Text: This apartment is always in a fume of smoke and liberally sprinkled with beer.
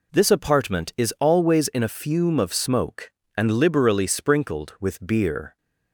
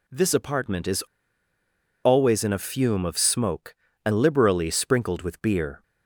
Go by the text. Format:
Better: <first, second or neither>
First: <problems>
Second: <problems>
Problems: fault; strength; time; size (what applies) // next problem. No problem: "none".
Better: first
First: none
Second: pauses between "is" and "always"; at 1.0 s; 1.0 s long